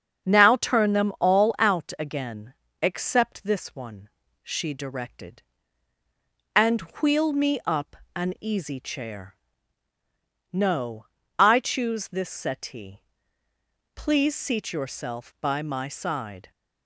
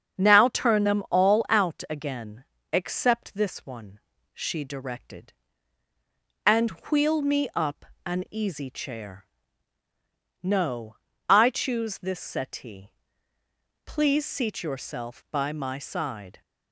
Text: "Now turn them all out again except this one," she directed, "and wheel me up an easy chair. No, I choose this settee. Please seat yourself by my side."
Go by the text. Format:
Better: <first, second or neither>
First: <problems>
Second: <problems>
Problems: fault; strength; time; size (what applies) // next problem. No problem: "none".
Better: neither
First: starts louder than the rest; strong; until 1.3 s; 7 dB // pauses between "again" and "except"; slight; at 2.5 s; 0.28 s long // pauses between "up" and "an"; slight; at 7.9 s; 0.16 s long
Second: starts louder than the rest; strong; until 1.2 s; 7 dB // pauses between "again" and "except"; slight; at 2.4 s; 0.28 s long // pauses between "up" and "an"; slight; at 7.8 s; 0.18 s long